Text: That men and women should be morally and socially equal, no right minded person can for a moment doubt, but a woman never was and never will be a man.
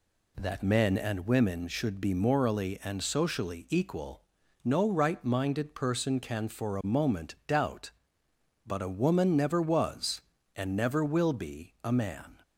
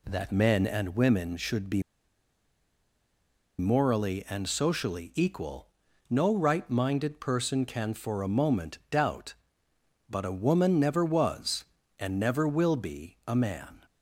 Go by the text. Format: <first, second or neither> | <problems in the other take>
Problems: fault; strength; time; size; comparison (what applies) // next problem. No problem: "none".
first | pauses between "be" and "morally"; strong; at 1.8 s; 1.7 s long